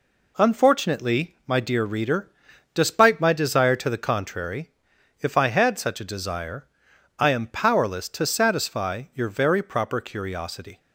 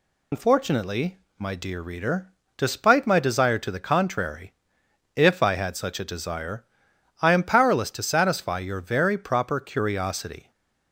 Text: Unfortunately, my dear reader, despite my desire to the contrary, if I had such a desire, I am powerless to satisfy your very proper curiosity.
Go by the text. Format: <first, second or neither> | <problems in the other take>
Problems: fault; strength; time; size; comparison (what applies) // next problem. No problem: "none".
first | loses the start of "Unfortunately"; at 0.3 s; 130 ms // stays silent after the last word; slight; from 10.4 s on; 0.5 s long